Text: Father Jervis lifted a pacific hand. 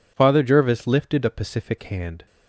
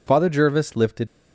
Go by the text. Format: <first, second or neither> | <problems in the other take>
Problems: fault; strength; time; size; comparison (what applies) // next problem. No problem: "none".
first | stops before "a pacific hand"; at 1.0 s